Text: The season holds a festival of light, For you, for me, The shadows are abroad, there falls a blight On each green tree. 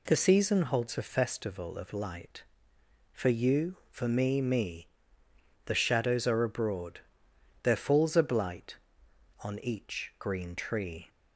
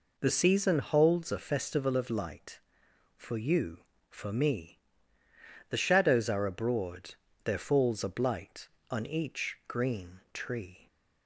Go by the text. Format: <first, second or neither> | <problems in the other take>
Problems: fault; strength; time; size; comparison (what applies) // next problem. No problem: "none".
second | says "me" twice; at 4.4 s